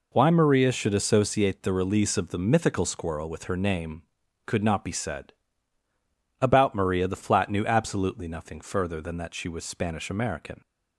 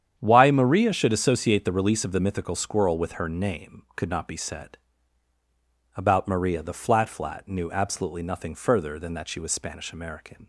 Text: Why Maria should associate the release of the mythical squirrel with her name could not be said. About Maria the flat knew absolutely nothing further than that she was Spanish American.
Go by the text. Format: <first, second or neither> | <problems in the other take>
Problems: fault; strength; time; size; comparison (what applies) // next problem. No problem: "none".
first | starts louder than the rest; strong; until 1.2 s; 9 dB // says "flat" twice; at 7.0 s